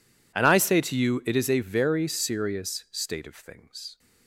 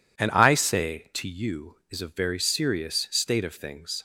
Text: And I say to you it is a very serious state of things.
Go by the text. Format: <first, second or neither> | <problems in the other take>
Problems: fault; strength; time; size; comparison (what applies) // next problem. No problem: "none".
first | skips "it"; at 1.8 s